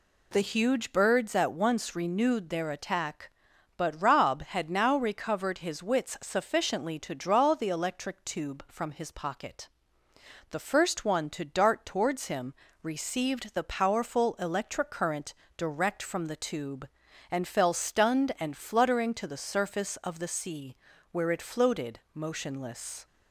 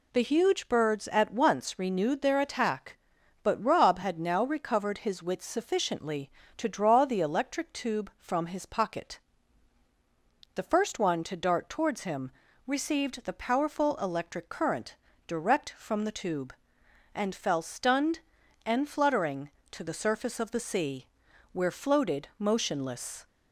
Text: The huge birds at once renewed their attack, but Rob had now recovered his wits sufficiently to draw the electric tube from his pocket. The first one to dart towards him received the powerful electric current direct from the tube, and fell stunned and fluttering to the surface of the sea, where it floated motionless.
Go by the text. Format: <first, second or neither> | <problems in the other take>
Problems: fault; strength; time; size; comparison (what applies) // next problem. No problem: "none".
first | pauses between "him" and "received"; slight; at 12.3 s; 0.34 s long; slight in the first // pauses between "current" and "direct"; slight; at 14.9 s; 0.32 s long; slight in the first // skips "it"; at 21.6 s